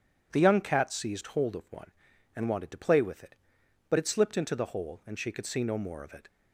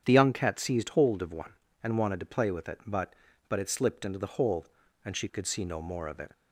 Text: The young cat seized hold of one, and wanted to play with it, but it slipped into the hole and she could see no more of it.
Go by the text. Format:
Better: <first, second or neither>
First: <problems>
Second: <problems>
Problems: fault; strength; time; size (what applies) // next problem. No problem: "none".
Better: first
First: none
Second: starts louder than the rest; strong; until 1.0 s; 8.5 dB // says "but" twice; at 3.4 s